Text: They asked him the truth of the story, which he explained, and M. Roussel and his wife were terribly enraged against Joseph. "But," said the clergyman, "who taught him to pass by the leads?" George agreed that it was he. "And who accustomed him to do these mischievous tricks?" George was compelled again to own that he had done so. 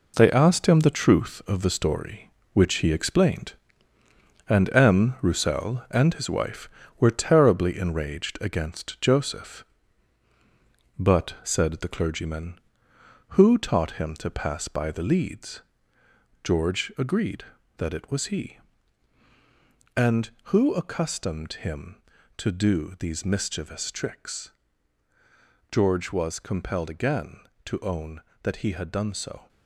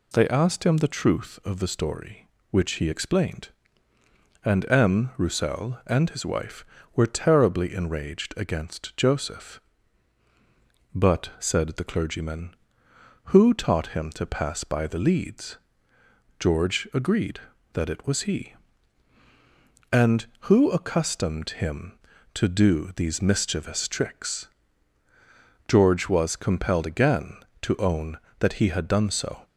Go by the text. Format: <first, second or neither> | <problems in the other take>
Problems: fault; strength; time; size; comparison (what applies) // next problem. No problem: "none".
second | gets quieter; strong; throughout; 8 dB